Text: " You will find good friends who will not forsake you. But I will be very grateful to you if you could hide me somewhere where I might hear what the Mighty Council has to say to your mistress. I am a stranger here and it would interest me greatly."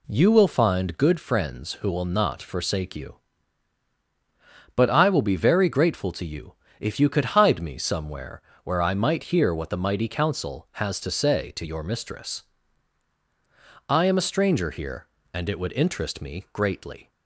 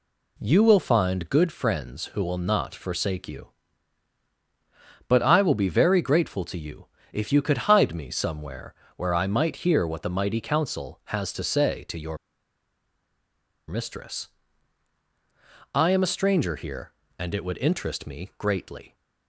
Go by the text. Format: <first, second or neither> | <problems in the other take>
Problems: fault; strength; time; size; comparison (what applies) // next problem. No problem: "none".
first | pauses between "you" and "if"; slight; at 6.8 s; 0.26 s long; slight in the first // pauses between "somewhere" and "where"; slight; at 8.7 s; 0.22 s long; slight in the first // pauses between "your" and "mistress"; strong; at 12.1 s; 1.5 s long